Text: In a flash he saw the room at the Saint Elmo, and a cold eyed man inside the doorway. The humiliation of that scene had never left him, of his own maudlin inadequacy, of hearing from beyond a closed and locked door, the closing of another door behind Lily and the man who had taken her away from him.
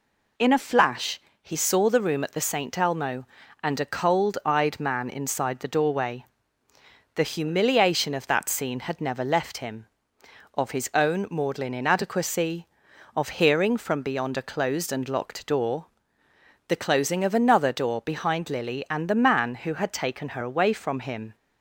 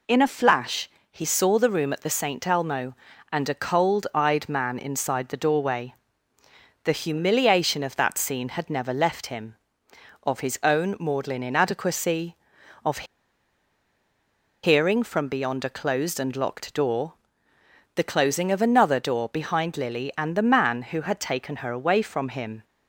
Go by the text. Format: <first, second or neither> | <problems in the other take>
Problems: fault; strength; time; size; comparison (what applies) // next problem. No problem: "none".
first | pauses between "flash" and "he"; slight; at 0.8 s; 0.22 s long; slight in the first // pauses between "of" and "hearing"; strong; at 13.0 s; 1.5 s long